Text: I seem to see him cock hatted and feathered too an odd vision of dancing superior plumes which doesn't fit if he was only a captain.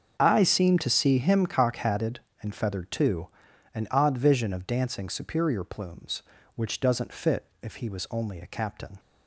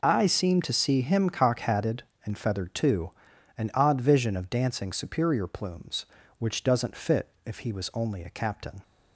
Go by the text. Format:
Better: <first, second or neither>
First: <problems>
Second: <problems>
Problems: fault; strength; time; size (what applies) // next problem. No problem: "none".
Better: second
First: starts louder than the rest; until 1.6 s; 6.5 dB // pauses between "too" and "an"; at 3.2 s; 0.44 s long // pauses between "fit" and "if"; slight; at 7.4 s; 0.16 s long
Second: pauses between "too" and "an"; at 3.1 s; 0.44 s long // pauses between "fit" and "if"; slight; at 7.3 s; 0.16 s long